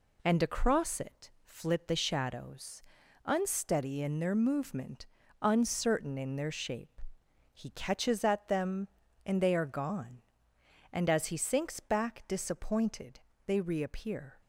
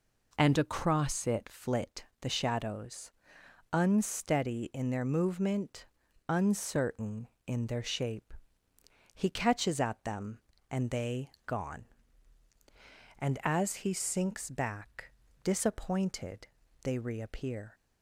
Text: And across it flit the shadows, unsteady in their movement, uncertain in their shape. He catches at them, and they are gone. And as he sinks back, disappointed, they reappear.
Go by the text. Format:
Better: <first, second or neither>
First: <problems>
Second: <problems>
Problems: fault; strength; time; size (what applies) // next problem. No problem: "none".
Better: first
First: none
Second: pauses between "flit" and "the"; slight; at 2.0 s; 0.18 s long // skips "are"; at 11.3 s